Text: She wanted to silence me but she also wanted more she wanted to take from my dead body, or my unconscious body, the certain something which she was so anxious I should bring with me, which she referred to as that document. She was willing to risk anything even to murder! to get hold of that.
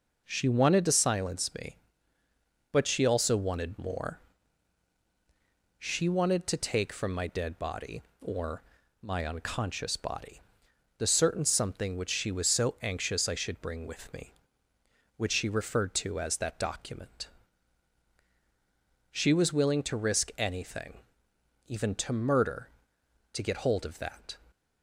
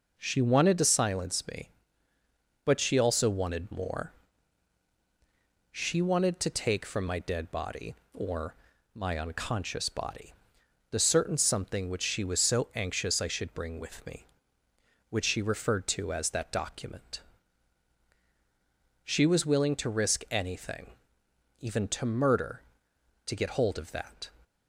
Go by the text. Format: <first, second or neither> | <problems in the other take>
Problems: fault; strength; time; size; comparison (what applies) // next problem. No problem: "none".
neither | pauses between "more" and "she"; strong; the same in both // pauses between "or" and "my"; the same in both // pauses between "anything" and "even"; noticeable; the same in both